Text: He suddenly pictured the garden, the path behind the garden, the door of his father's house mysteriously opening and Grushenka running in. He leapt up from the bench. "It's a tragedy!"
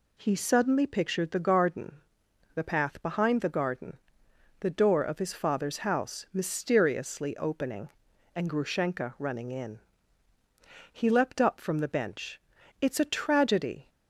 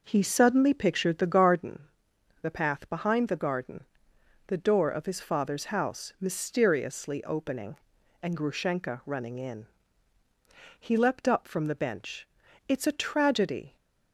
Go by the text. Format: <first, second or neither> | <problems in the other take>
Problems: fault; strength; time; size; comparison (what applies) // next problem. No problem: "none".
first | starts louder than the rest; noticeable; until 1.7 s; 5.5 dB